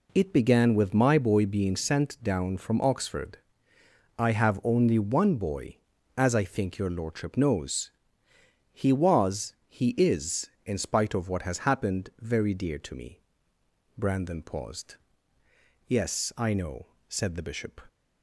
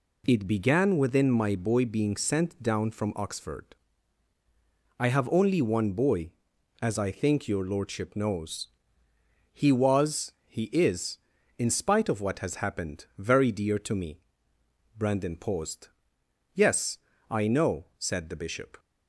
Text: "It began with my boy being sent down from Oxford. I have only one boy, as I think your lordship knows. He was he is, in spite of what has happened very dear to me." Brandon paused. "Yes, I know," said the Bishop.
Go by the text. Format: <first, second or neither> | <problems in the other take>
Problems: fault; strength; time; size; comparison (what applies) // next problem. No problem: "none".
first | says "within" for "with"; at 0.9 s // pauses between "was" and "he"; slight; at 10.3 s; 0.16 s long; slight in the first